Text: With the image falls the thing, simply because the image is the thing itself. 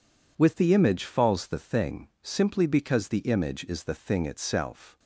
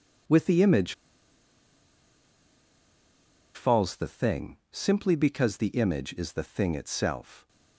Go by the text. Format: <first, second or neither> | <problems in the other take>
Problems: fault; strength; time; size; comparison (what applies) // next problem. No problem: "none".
first | pauses between "image" and "falls"; strong; at 0.9 s; 2.6 s long